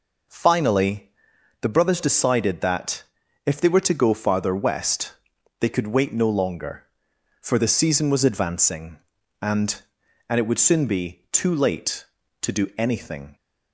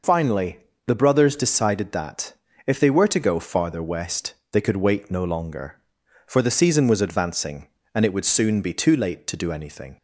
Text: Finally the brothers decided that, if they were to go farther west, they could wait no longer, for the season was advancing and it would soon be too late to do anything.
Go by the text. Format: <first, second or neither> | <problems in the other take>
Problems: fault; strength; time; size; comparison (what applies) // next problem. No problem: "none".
second | pauses between "Finally" and "the"; noticeable; at 1.1 s; 0.50 s long; slight in the second // says "and" twice; at 10.2 s